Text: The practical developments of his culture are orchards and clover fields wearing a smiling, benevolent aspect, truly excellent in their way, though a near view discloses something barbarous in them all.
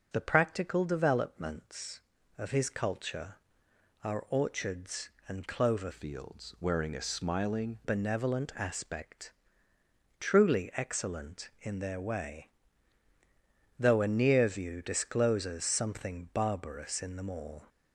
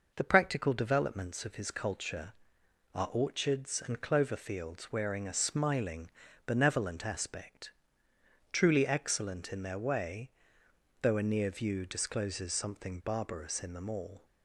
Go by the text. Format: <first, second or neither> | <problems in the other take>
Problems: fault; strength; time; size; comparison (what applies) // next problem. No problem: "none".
second | changes voice from "fields" to "smiling"; from 5.9 to 7.7 s; 1.8 s long